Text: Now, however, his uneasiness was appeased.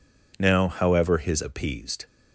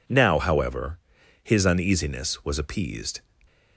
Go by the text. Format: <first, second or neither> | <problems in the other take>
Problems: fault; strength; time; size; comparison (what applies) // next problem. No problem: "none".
second | skips "uneasiness was"; at 1.4 s